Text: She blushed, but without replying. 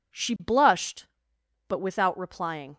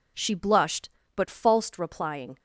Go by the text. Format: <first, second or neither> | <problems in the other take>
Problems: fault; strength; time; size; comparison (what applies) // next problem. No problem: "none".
first | says "falsed" for "without"; at 1.2 s